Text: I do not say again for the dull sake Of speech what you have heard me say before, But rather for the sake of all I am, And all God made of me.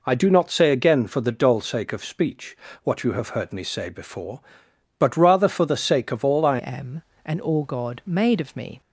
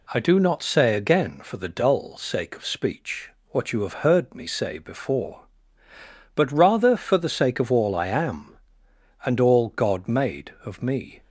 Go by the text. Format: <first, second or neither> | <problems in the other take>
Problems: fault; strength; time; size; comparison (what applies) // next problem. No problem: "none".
second | pauses between "speech" and "what"; slight; at 2.5 s; 0.24 s long; slight in the second // changes voice at "am"; from 6.5 s on; 2.3 s long